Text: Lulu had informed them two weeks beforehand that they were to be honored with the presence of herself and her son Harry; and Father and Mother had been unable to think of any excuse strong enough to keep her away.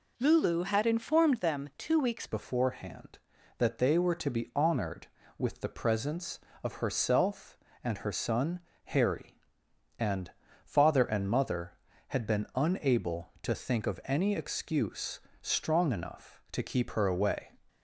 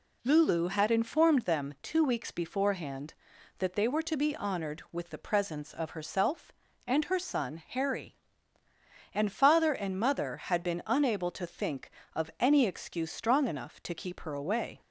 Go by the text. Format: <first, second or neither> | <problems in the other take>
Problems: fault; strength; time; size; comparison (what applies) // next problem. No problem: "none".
second | changes voice at "beforehand"; from 2.2 s on; 15.3 s long // pauses between "son" and "Harry"; slight; at 8.5 s; 0.26 s long // pauses between "and" and "Father"; slight; at 10.3 s; 0.34 s long // pauses between "excuse" and "strong"; slight; at 15.1 s; 0.22 s long